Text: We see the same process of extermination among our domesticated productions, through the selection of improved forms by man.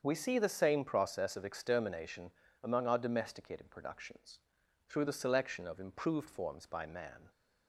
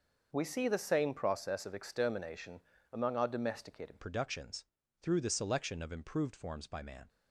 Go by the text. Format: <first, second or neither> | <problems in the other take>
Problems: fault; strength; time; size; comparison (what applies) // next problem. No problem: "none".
first | starts louder than the rest; until 1.3 s; 6 dB; strong in the first // pauses between "extermination" and "among"; slight; at 2.6 s; 0.32 s long; slight in the first // changes voice at "productions"; from 4.0 s on; 3.0 s long